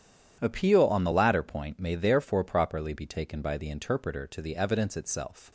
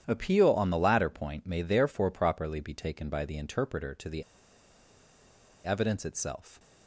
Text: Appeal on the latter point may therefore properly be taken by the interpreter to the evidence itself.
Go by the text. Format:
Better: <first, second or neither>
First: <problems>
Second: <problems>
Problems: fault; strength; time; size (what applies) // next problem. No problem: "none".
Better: first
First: starts louder than the rest; strong; until 1.4 s; 9.5 dB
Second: starts louder than the rest; strong; until 1.0 s; 9.5 dB // pauses between "the" and "evidence"; strong; at 4.2 s; 1.4 s long